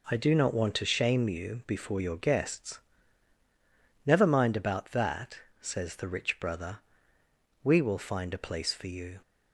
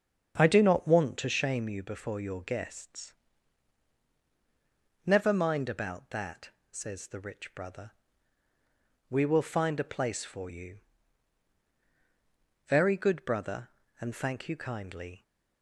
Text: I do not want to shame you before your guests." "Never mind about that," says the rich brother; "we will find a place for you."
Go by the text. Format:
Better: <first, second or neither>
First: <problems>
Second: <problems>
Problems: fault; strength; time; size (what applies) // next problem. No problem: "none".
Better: first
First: none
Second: starts louder than the rest; strong; until 1.4 s; 7.5 dB // goes on to say "Very good brother and thank you kindly"; strong; from 12.6 s on; 2.5 s long